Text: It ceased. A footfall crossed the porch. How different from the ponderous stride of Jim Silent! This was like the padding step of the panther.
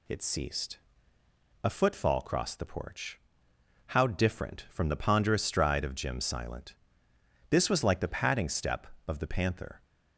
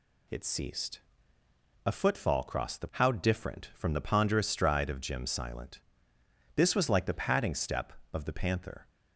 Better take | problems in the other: first | skips "porch"; at 2.9 s

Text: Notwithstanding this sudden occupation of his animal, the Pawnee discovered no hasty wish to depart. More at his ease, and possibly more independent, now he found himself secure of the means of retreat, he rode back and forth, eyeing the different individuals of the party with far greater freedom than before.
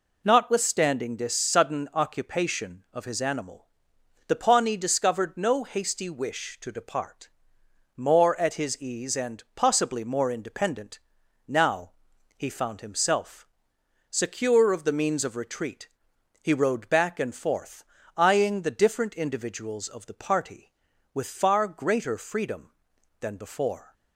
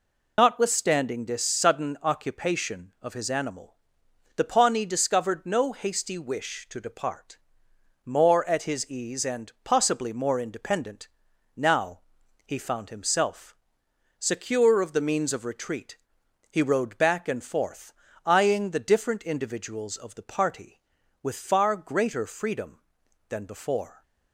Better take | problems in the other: first | loses the start of "Notwithstanding"; at 0.3 s; 40 ms // pauses between "now" and "he"; noticeable; at 11.9 s; 0.46 s long; noticeable in the first // pauses between "himself" and "secure"; noticeable; at 13.5 s; 0.64 s long; noticeable in the first

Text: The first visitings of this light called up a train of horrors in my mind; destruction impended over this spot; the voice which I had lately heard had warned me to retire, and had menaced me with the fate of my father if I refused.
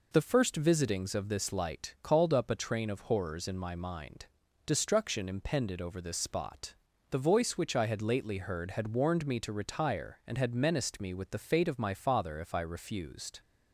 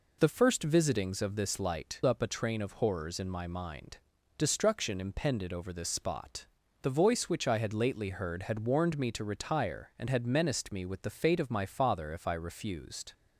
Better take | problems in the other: first | skips "called"; at 2.0 s

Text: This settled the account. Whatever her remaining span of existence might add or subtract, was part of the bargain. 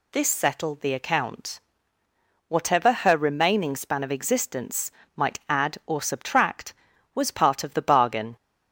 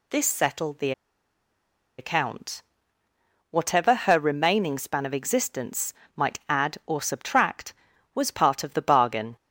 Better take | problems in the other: first | pauses between "the" and "account"; at 0.9 s; 1.0 s long // pauses between "existence" and "might"; slight; at 5.9 s; 0.24 s long; slight in the first

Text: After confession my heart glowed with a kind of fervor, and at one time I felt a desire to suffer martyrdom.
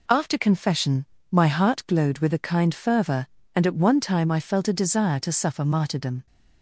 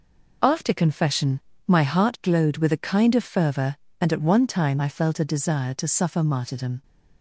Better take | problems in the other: second | pauses between "confession" and "my"; slight; at 1.0 s; 0.28 s long; slight in the second // skips "of"; at 2.7 s

